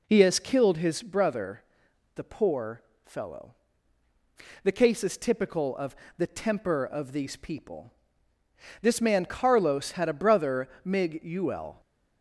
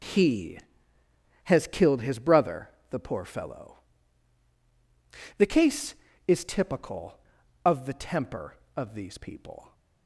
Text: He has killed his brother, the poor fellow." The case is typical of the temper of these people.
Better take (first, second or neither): second